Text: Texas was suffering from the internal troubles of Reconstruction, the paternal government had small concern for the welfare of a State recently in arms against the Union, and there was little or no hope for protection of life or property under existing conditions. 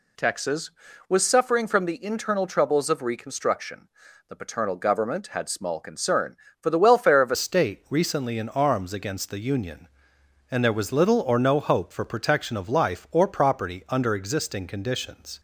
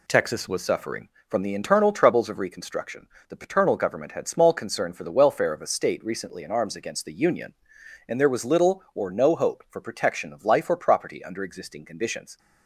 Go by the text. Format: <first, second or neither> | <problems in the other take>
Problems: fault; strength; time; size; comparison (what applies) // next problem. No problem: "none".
second | changes voice at "State"; from 7.3 s on; 8.0 s long